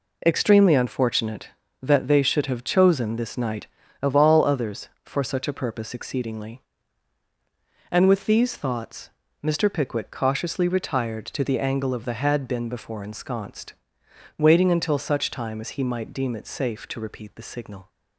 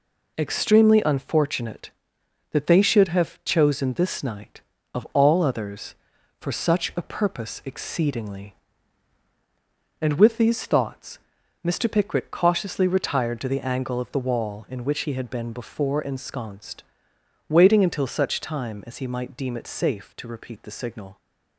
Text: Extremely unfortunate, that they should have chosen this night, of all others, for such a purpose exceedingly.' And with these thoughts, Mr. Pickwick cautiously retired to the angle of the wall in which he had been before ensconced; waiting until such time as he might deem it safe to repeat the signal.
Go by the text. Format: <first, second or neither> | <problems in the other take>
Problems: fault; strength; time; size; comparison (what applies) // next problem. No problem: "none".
second | skips "wall in which he"; at 12.1 s